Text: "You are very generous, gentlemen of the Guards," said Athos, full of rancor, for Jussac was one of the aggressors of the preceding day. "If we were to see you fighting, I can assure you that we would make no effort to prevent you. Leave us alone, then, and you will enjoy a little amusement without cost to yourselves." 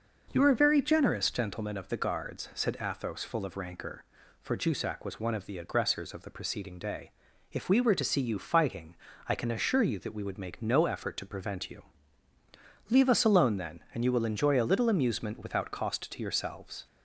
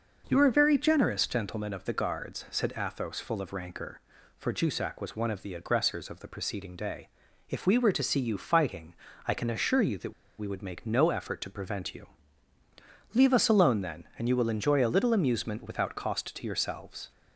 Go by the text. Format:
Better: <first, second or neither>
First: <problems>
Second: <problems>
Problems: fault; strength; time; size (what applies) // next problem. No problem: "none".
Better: first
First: none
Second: pauses between "that" and "we"; slight; at 10.1 s; 0.25 s long